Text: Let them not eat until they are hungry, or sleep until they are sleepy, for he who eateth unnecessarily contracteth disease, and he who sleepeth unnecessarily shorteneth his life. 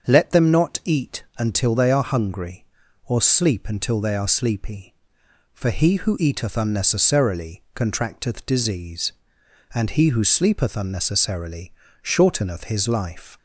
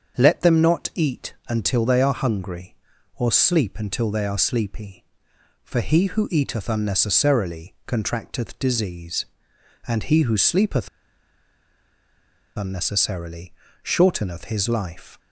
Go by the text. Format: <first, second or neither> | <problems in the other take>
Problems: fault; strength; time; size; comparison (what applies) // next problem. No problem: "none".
first | starts louder than the rest; until 1.2 s; 6.5 dB; also in the first // pauses between "sleepeth" and "unnecessarily"; strong; at 10.8 s; 1.6 s long // pauses between "unnecessarily" and "shorteneth"; slight; at 13.5 s; 0.30 s long; slight in the first